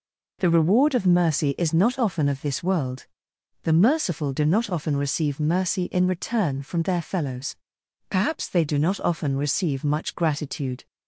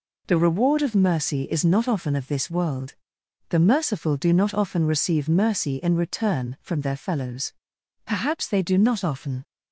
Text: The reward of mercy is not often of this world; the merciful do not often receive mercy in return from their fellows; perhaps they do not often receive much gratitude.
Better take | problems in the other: first | stops before "receive much gratitude"; at 9.4 s

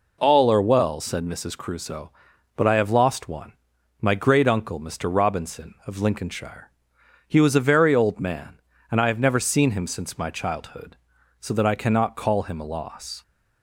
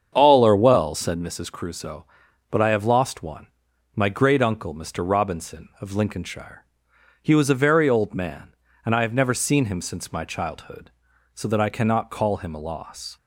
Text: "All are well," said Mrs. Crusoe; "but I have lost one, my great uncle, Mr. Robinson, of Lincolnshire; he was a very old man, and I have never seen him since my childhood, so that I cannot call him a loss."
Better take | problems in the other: first | starts louder than the rest; strong; until 1.2 s; 7.5 dB

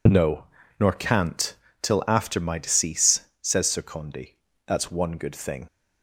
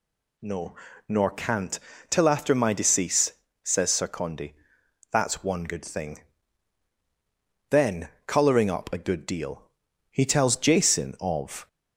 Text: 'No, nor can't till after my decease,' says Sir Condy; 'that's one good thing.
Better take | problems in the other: first | pauses between "can't" and "till"; slight; at 1.7 s; 0.30 s long; slight in the first // goes on to say "Then colouring up a good deal he tells Jason of"; strong; from 7.6 s on; 3.9 s long

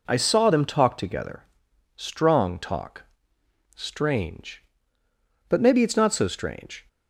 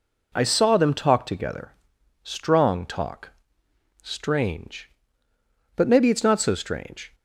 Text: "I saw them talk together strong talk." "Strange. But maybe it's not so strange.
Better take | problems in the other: neither | pauses between "together" and "strong"; noticeable; the same in both

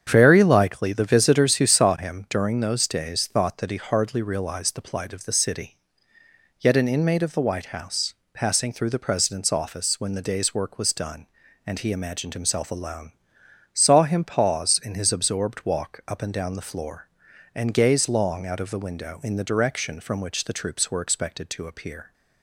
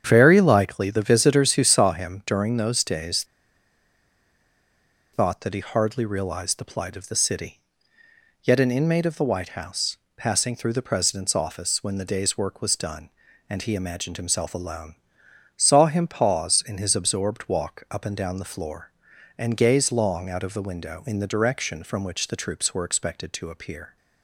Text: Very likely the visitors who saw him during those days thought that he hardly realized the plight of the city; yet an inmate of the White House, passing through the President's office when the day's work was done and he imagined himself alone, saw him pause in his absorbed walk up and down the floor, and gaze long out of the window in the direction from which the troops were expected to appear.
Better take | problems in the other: first | starts louder than the rest; strong; until 1.0 s; 8 dB; strong in the first // pauses between "days" and "thought"; strong; at 3.2 s; 1.8 s long

